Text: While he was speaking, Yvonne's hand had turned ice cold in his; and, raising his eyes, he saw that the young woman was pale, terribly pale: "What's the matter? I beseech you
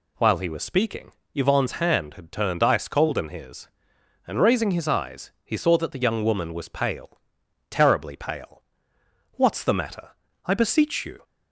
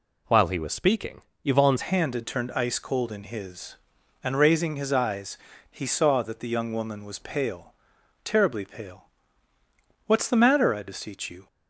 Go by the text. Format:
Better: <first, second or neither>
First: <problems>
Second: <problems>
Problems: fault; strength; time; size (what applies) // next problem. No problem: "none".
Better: first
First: none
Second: changes voice at "hand"; from 1.8 s on; 9.6 s long